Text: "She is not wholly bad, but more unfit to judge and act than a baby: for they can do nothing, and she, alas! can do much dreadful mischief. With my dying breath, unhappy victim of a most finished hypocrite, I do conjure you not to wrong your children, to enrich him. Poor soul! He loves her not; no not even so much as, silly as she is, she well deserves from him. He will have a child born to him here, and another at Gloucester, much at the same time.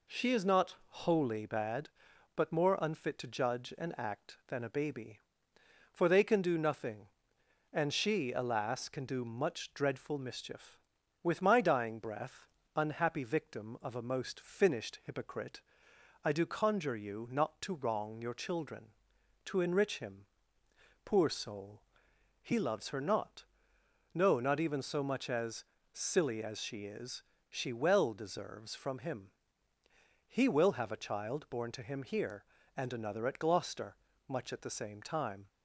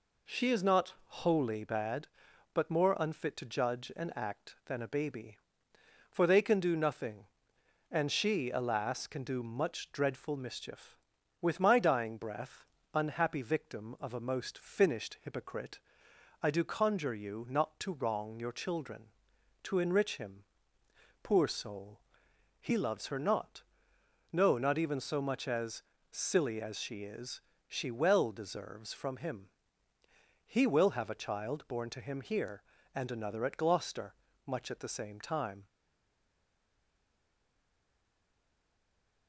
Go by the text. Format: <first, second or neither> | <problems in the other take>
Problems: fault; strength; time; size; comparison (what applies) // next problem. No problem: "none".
first | stays silent after the last word; strong; from 35.6 s on; 3.6 s long